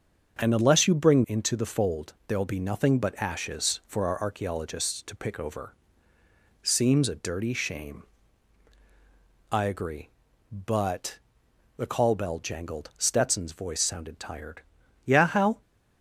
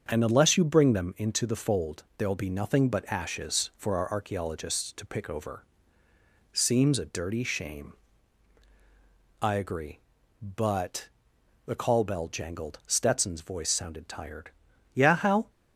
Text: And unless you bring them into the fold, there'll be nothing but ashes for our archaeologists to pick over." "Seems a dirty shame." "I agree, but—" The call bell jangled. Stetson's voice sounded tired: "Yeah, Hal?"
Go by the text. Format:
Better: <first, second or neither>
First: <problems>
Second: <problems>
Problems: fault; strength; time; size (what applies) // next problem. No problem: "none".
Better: second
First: starts louder than the rest; until 1.4 s; 7 dB // skips "them"; at 1.2 s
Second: starts louder than the rest; until 1.0 s; 7 dB